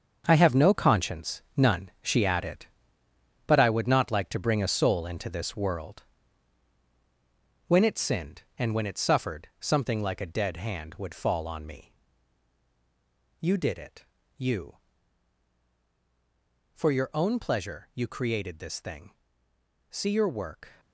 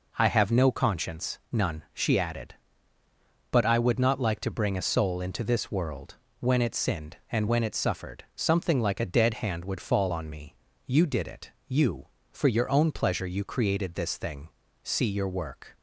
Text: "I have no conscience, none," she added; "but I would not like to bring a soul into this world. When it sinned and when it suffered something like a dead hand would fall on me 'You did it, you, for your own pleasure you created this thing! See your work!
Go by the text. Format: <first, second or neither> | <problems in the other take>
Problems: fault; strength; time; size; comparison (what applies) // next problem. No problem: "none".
second | gets quieter; strong; throughout; 10.5 dB // pauses between "me" and "You"; strong; at 11.9 s; 1.4 s long; slight in the second